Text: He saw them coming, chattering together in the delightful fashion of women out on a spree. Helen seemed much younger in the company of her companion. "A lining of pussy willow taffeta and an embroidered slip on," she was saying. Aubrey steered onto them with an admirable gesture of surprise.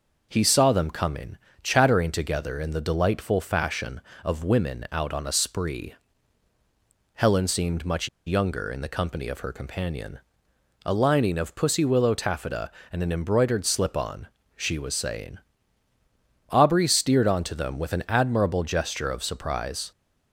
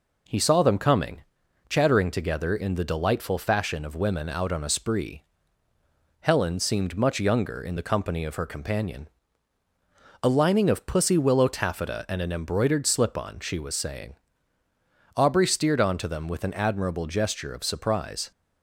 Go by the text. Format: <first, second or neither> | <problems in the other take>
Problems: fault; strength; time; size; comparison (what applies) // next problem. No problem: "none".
second | pauses between "much" and "younger"; slight; at 8.0 s; 0.18 s long